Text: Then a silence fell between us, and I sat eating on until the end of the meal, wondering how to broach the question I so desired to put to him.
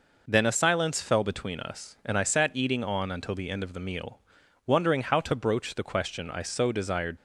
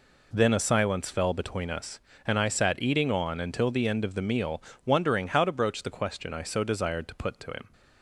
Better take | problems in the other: second | stops before "to put to him"; at 7.1 s

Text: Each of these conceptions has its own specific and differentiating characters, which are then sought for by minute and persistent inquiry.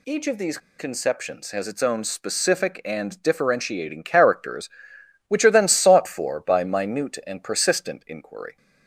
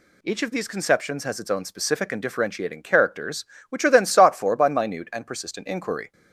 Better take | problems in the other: second | pauses between "these" and "conceptions"; slight; at 0.5 s; 0.20 s long

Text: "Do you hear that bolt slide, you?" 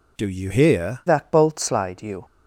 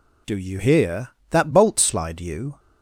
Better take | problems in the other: second | changes voice at "that"; from 1.0 s on; 1.2 s long

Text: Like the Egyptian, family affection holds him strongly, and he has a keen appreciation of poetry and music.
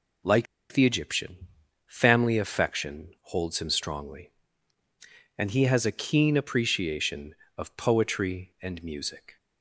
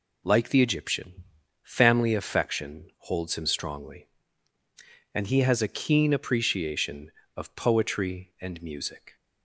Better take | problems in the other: second | pauses between "Like" and "the"; slight; at 0.4 s; 0.26 s long

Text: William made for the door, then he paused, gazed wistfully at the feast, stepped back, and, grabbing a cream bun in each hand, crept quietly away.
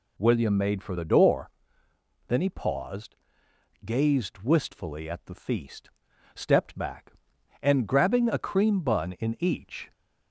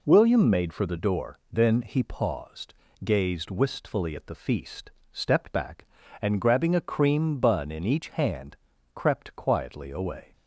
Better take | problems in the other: second | stops before "hand crept quietly away"; at 9.9 s

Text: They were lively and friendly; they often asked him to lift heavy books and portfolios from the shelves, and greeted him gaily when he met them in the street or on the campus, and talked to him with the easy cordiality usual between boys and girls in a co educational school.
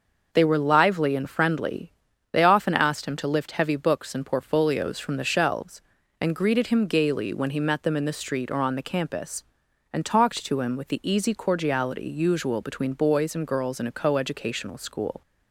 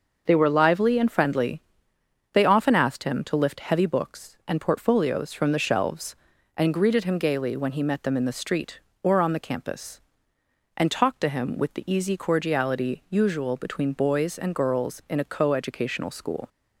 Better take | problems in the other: neither | starts louder than the rest; the same in both

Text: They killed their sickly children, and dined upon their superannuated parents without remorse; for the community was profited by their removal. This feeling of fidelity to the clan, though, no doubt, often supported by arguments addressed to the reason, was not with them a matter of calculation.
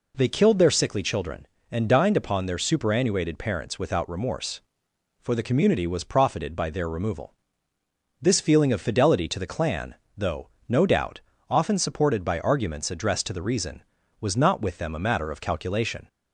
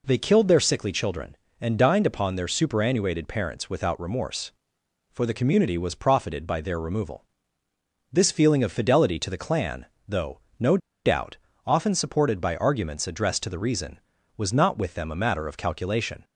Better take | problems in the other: first | pauses between "no" and "doubt"; slight; at 10.7 s; 0.27 s long

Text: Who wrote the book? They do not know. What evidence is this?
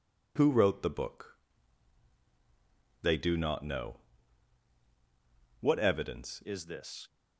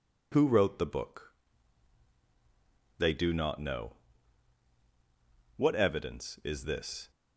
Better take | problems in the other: second | changes voice at "is"; from 6.4 s on; 0.6 s long

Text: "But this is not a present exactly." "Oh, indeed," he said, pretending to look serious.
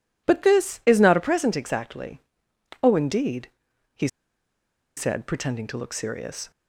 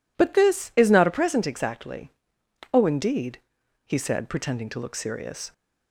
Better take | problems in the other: second | pauses between "he" and "said"; noticeable; at 4.0 s; 0.89 s long

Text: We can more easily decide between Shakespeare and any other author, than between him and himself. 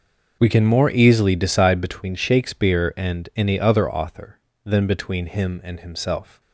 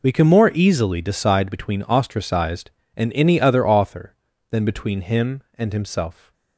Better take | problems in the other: first | says "Ostracized" for "Shakespeare"; at 1.8 s

